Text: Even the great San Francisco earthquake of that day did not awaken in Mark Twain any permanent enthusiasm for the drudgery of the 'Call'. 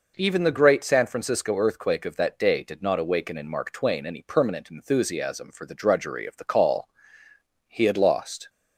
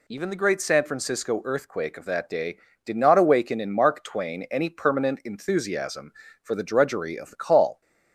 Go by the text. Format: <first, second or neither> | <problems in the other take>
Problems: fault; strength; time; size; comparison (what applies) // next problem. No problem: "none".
second | goes on to say "He had lost"; noticeable; from 7.6 s on; 0.82 s long